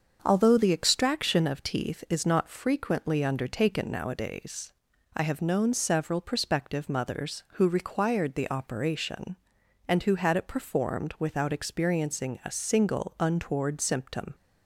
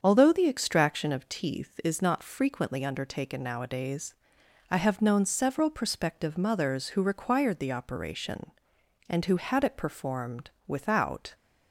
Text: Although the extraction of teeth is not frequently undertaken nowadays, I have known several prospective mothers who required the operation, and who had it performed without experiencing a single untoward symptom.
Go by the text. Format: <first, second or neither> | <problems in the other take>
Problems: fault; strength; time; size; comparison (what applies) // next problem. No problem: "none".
first | starts louder than the rest; strong; until 1.0 s; 7 dB; also in the first // pauses between "performed" and "without"; slight; at 10.4 s; 0.18 s long // stops before "experiencing a single untoward symptom"; at 11.3 s